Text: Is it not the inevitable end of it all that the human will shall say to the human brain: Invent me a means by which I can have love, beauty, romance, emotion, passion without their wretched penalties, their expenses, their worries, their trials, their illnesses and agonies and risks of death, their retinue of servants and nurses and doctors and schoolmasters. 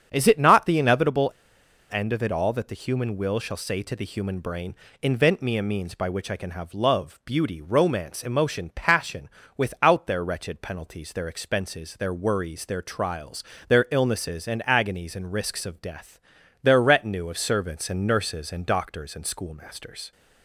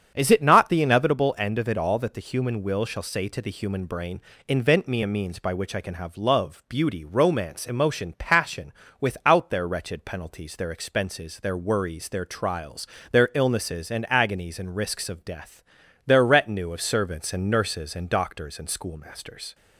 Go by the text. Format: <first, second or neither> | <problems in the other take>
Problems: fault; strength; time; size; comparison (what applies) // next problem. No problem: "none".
second | starts louder than the rest; strong; until 1.1 s; 8 dB; strong in the second // pauses between "inevitable" and "end"; noticeable; at 1.2 s; 0.63 s long // pauses between "passion" and "without"; slight; at 9.2 s; 0.26 s long; slight in the second